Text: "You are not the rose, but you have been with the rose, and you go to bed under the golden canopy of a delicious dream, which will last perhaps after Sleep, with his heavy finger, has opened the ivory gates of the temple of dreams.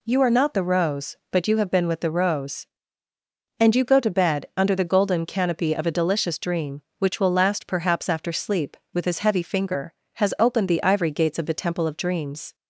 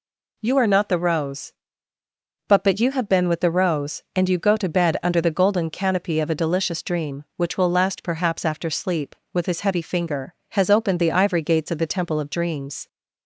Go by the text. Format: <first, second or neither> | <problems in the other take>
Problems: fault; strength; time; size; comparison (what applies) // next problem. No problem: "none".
first | says "but" twice; at 2.6 s